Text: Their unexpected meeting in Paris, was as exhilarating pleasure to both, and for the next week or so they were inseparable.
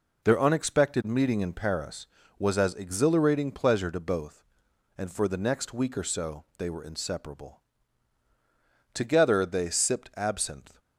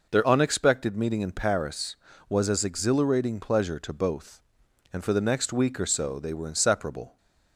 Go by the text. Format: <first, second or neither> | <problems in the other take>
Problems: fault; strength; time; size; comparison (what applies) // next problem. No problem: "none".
second | goes on to say "Together they sipped absinthe"; strong; from 8.9 s on; 1.8 s long